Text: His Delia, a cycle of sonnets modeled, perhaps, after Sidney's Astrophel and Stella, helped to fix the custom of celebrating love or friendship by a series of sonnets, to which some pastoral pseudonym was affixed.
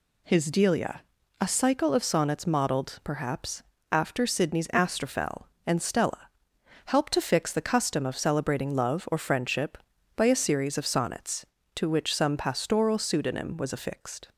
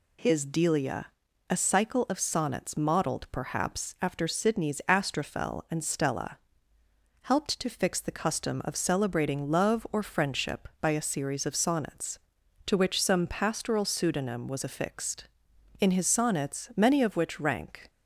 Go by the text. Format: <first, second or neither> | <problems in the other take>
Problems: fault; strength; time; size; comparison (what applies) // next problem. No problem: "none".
first | goes on to say "In his sonnets many of which rank"; strong; from 15.7 s on; 2.1 s long